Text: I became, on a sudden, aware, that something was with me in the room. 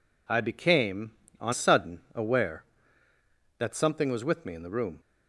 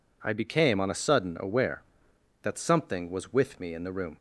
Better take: second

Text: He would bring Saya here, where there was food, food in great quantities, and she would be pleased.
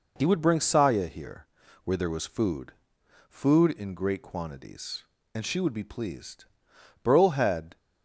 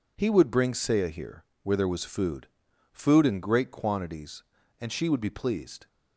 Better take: second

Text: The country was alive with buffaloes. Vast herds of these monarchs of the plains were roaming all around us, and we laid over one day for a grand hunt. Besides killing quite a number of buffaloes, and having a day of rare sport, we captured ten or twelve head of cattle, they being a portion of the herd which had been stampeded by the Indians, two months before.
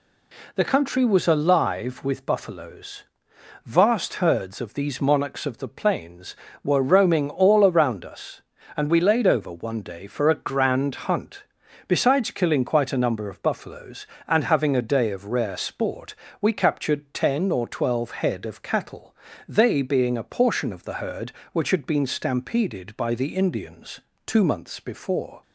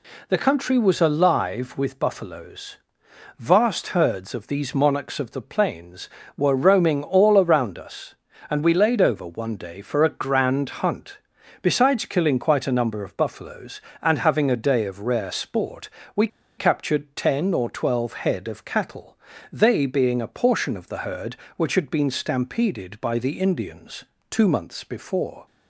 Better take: first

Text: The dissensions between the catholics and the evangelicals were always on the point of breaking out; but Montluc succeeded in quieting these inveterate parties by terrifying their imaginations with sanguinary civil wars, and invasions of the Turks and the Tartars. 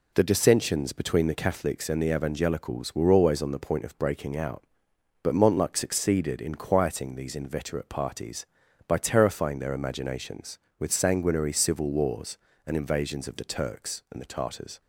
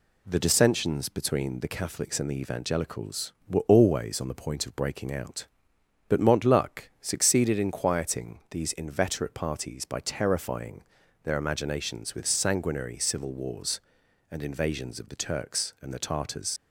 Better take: first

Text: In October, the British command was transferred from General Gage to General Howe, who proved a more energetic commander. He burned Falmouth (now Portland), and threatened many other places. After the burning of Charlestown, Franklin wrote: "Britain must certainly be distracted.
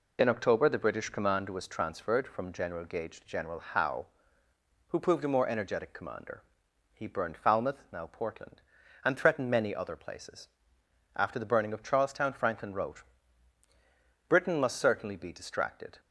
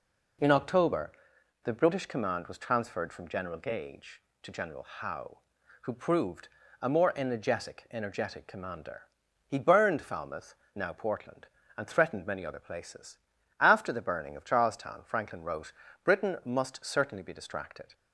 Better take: first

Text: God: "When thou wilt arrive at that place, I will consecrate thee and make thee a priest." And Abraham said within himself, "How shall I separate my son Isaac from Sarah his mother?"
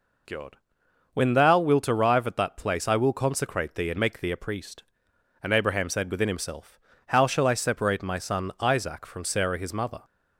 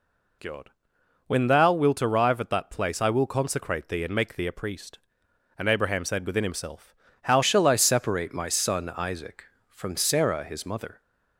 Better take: first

